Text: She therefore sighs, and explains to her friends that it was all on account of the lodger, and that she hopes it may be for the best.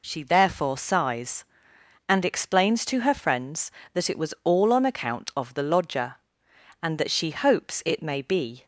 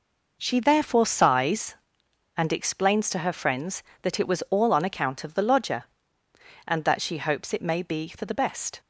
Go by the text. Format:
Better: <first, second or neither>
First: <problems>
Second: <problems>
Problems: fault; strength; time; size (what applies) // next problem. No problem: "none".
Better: second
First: stops before "for the best"; at 8.6 s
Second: none